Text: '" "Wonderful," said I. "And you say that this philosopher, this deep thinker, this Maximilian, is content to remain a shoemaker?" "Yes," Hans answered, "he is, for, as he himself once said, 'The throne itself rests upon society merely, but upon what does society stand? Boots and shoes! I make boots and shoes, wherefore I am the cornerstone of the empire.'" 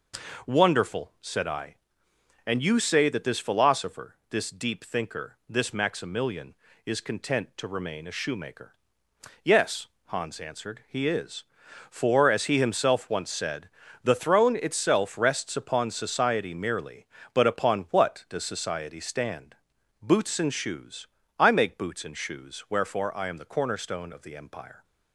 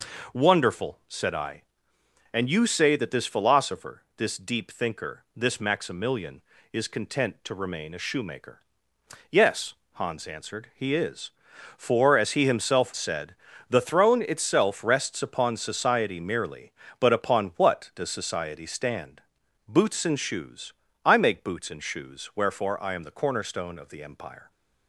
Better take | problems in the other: first | skips "once"; at 12.9 s

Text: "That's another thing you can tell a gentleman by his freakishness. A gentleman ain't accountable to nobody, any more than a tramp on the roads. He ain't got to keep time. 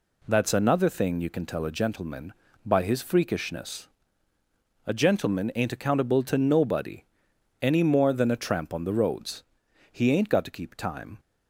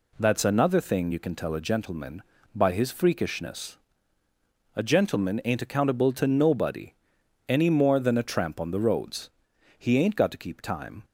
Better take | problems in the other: neither | none

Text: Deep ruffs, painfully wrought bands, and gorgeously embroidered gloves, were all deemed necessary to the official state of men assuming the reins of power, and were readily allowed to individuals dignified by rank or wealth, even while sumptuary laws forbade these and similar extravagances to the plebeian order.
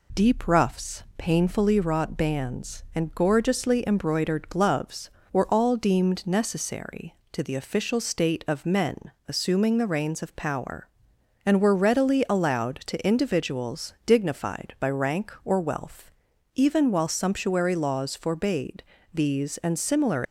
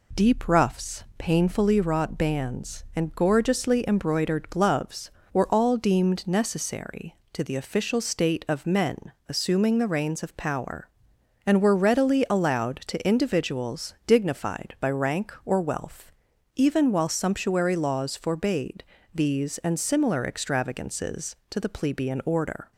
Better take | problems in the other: second | pauses between "men" and "assuming"; slight; at 9.1 s; 0.16 s long; slight in the second // pauses between "forbade" and "these"; slight; at 18.8 s; 0.30 s long; slight in the second // stops before "extravagances to the plebeian order"; at 20.2 s

